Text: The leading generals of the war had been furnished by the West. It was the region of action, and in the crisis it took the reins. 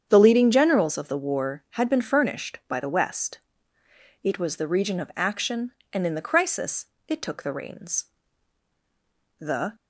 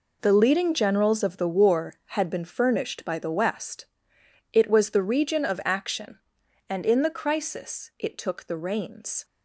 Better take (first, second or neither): second